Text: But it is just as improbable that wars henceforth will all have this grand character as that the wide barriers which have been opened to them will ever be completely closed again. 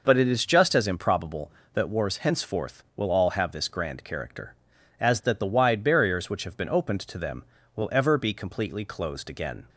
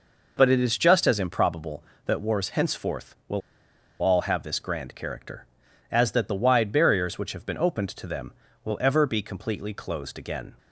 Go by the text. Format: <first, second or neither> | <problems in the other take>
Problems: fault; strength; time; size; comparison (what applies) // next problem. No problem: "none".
first | pauses between "will" and "all"; noticeable; at 3.4 s; 0.60 s long